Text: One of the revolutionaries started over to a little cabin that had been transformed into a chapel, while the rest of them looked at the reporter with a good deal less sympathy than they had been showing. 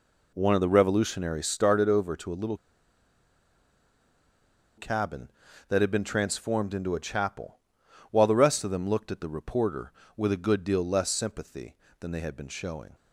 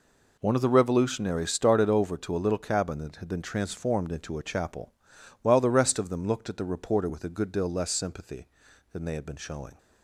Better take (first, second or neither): second